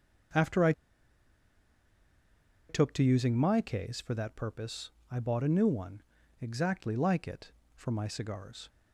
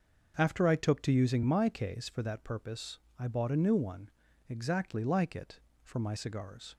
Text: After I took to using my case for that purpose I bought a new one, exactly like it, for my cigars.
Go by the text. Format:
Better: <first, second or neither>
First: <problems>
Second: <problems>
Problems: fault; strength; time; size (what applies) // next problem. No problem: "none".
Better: second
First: starts louder than the rest; until 3.3 s; 6.5 dB // pauses between "I" and "took"; strong; at 0.7 s; 1.9 s long // pauses between "purpose" and "I"; slight; at 4.9 s; 0.18 s long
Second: starts louder than the rest; until 1.3 s; 6.5 dB // pauses between "purpose" and "I"; slight; at 2.9 s; 0.18 s long